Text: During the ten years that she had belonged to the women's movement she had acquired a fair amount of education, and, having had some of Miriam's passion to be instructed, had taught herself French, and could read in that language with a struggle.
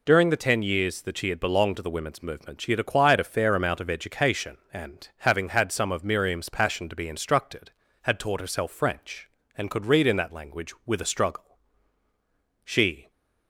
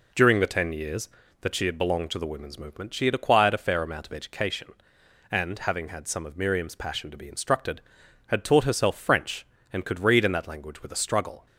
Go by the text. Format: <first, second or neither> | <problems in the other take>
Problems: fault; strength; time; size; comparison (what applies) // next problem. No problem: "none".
second | goes on to say "She"; slight; from 12.6 s on; 0.46 s long